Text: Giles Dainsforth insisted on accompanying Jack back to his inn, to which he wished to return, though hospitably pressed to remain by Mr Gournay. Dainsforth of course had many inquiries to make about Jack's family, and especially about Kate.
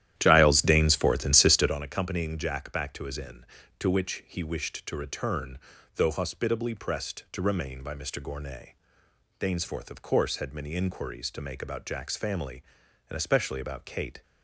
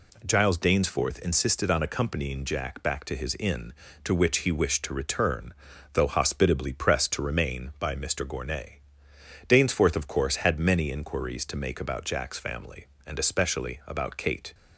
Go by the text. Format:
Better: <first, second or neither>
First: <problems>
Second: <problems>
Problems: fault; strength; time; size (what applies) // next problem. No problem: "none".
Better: second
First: starts louder than the rest; strong; until 1.8 s; 12 dB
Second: none